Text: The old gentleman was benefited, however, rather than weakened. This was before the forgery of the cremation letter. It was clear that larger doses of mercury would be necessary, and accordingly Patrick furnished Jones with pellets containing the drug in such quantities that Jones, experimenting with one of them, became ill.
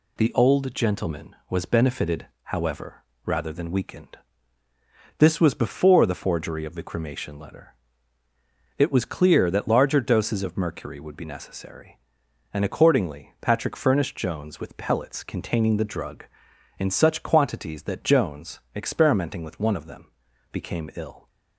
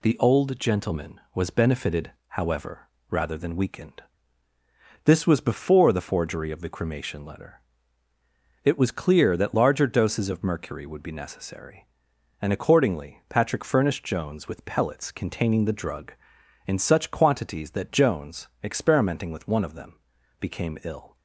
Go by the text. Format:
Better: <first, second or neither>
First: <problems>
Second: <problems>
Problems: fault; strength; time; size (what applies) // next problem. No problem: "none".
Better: neither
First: none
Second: none